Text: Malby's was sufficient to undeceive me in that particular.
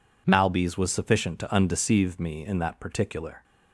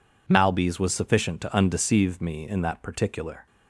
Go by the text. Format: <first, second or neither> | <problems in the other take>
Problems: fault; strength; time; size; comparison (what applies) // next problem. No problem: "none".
neither | none